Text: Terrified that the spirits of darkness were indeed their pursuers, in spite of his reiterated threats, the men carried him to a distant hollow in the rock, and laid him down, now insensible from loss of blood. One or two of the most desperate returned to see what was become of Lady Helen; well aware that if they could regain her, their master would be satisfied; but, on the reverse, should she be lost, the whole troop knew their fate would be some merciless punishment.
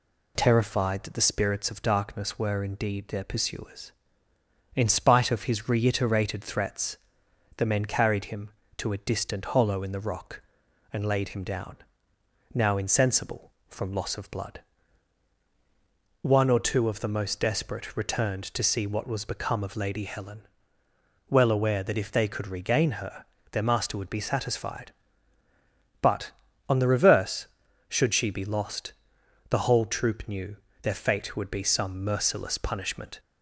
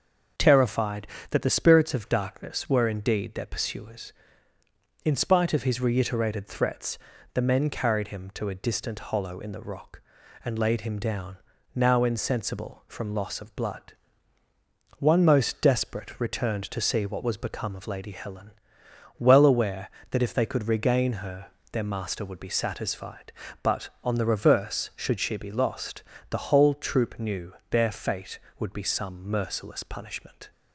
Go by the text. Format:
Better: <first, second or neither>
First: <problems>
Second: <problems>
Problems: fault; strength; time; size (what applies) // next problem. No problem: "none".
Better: first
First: pauses between "knew" and "their"; slight; at 30.5 s; 0.26 s long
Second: starts louder than the rest; until 1.6 s; 6 dB // skips "or two of the"; at 15.2 s // pauses between "knew" and "their"; slight; at 27.5 s; 0.18 s long